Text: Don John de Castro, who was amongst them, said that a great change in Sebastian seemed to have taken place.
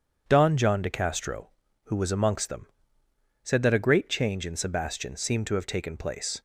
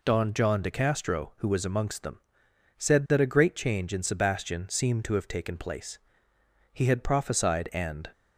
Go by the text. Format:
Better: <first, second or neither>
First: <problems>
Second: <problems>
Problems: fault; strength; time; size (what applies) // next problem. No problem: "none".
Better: first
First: none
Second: goes on to say "He had prophesied and"; from 6.7 s on; 1.3 s long